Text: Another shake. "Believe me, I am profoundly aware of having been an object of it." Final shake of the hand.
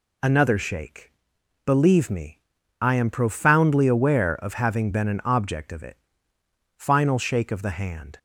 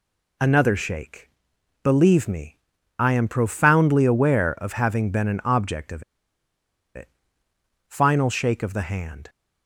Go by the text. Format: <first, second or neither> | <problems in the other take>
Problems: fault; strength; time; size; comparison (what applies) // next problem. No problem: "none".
first | pauses between "of" and "it"; noticeable; at 6.0 s; 0.91 s long